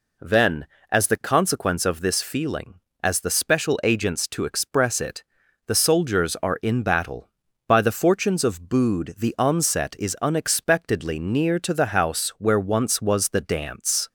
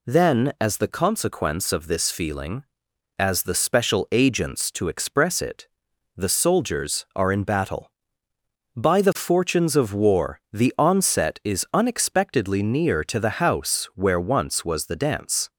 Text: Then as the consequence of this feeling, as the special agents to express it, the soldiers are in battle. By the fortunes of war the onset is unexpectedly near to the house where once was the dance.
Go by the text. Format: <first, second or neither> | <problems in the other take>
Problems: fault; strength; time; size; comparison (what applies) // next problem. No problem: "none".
second | says "bood" for "war"; at 8.6 s